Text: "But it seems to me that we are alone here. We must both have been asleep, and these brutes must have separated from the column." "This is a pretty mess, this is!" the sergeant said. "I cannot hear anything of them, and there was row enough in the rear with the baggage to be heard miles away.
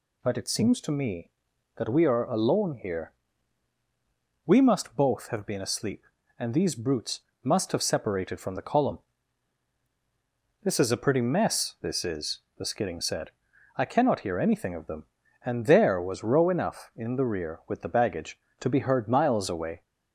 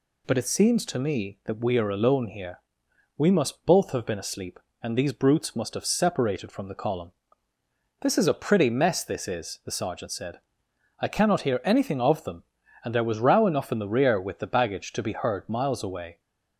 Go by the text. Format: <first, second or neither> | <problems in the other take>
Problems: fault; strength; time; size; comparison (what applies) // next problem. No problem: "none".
second | pauses between "brutes" and "must"; slight; at 7.2 s; 0.24 s long // says "skidding" for "sergeant"; at 12.6 s